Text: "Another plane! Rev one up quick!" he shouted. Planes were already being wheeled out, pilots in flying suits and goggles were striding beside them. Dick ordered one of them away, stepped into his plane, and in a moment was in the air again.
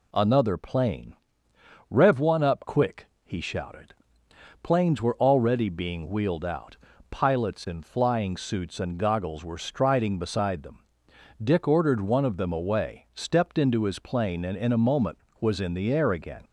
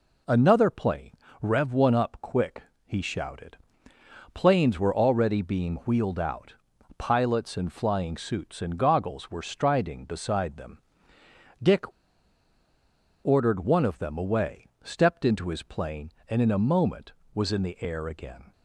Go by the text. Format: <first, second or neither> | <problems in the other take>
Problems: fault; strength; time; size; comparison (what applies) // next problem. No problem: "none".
first | pauses between "Dick" and "ordered"; strong; at 11.8 s; 1.3 s long